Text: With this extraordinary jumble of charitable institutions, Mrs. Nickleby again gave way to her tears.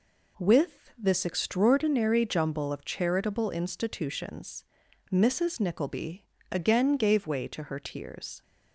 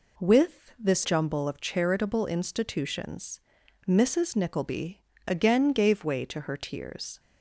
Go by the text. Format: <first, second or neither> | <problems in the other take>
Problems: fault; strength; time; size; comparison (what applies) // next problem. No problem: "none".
first | skips "extraordinary"; at 1.0 s // pauses between "Nickleby" and "again"; slight; at 5.0 s; 0.24 s long; slight in the first